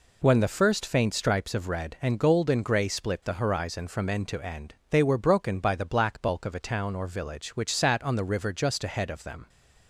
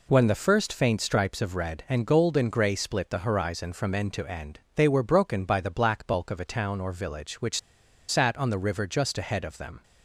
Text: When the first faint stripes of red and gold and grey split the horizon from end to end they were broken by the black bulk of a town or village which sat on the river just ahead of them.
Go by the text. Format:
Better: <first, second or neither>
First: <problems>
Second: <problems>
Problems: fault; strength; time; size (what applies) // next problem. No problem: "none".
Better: first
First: pauses between "end" and "they"; slight; at 4.7 s; 0.16 s long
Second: pauses between "end" and "they"; slight; at 4.5 s; 0.16 s long // pauses between "which" and "sat"; noticeable; at 7.5 s; 0.49 s long